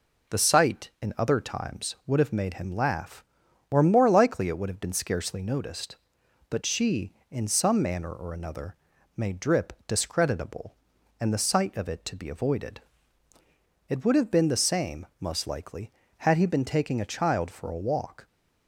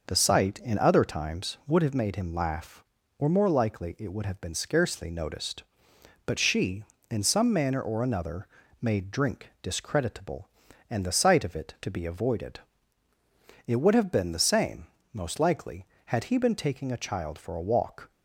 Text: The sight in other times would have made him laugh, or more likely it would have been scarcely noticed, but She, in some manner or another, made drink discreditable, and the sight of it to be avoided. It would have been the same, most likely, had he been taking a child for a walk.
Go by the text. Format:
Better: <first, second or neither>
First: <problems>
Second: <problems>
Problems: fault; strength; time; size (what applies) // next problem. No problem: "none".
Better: second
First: says "drip" for "drink"; at 9.3 s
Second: none